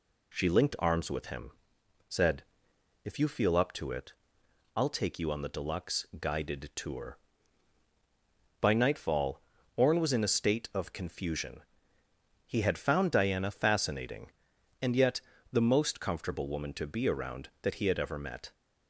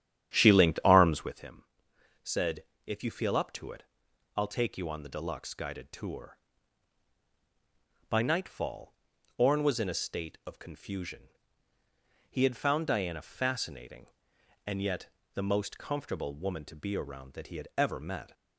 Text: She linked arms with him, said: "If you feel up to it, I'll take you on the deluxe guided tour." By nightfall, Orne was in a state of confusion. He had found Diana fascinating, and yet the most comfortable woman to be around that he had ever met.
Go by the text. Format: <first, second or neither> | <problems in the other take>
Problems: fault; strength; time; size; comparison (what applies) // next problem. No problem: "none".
first | starts louder than the rest; strong; until 1.4 s; 10.5 dB // pauses between "yet" and "the"; slight; at 15.0 s; 0.26 s long; slight in the first